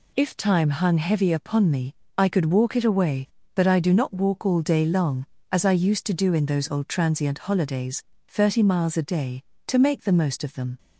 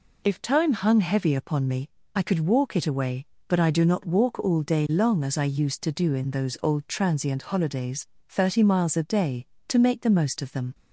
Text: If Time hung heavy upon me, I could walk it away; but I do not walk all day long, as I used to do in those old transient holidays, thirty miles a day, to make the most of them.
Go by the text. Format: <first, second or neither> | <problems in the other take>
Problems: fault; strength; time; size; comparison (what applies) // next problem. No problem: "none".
neither | none